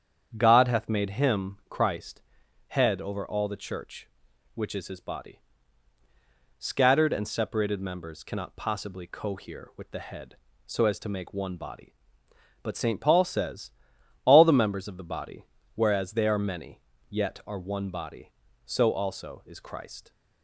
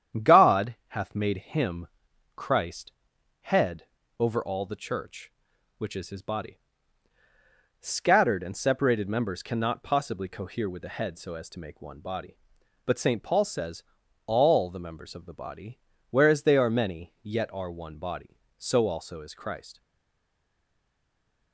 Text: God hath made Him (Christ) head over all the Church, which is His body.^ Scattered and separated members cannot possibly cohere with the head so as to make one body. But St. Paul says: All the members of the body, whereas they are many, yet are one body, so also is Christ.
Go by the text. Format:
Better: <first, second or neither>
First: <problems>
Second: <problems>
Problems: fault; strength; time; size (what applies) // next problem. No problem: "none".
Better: first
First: starts louder than the rest; strong; until 1.3 s; 8 dB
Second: starts louder than the rest; strong; until 1.3 s; 9 dB // pauses between "head" and "over"; slight; at 3.8 s; 0.36 s long // stays silent after the last word; noticeable; from 19.8 s on; 1.7 s long